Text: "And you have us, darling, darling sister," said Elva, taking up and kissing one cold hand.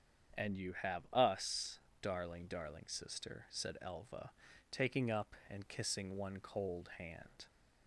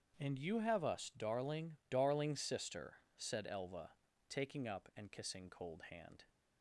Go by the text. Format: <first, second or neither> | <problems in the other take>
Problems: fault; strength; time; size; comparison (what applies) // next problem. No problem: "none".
first | starts louder than the rest; strong; until 1.2 s; 7.5 dB; strong in the first // skips "one"; at 5.4 s